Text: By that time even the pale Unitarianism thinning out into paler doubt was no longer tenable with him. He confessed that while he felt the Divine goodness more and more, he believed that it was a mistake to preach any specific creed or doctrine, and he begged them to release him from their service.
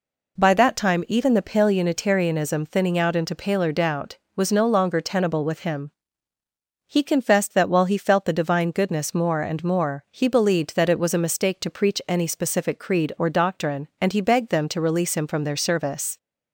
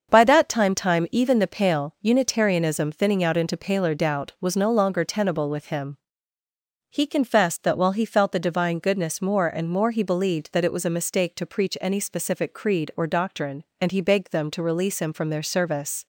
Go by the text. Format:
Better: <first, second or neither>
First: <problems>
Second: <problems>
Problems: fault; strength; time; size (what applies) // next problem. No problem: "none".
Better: first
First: none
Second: starts louder than the rest; until 1.1 s; 7 dB // says "time" twice; at 0.7 s